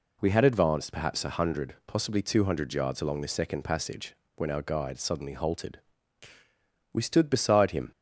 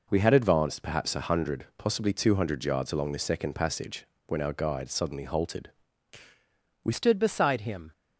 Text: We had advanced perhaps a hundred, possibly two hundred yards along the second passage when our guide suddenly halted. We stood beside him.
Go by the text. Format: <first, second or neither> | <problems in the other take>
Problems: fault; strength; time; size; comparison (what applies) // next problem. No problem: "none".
first | pauses between "passage" and "when"; slight; at 4.0 s; 0.20 s long; slight in the first // changes voice at "stood"; from 6.9 s on; 1.0 s long